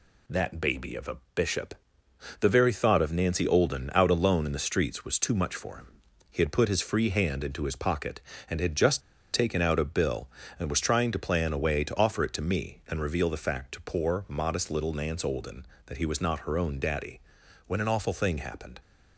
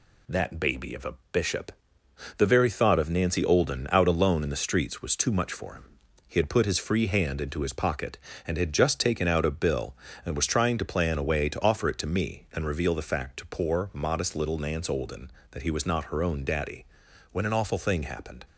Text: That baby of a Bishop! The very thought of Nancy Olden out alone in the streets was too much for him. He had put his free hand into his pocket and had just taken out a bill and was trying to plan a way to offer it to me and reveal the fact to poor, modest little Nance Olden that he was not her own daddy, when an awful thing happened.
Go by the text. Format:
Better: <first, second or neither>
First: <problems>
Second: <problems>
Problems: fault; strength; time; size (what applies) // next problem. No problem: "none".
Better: second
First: pauses between "a" and "Bishop"; slight; at 1.1 s; 0.18 s long // pauses between "just" and "taken"; slight; at 9.0 s; 0.33 s long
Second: pauses between "a" and "Bishop"; slight; at 1.1 s; 0.18 s long